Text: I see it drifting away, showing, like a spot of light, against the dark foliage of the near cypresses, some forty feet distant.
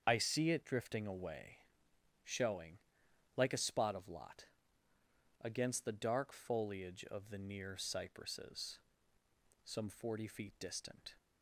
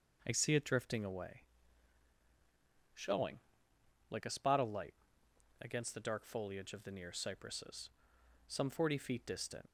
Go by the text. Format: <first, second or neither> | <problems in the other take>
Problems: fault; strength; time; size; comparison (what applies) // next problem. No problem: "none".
second | starts louder than the rest; strong; until 1.0 s; 7.5 dB // says "lot" for "light"; at 4.0 s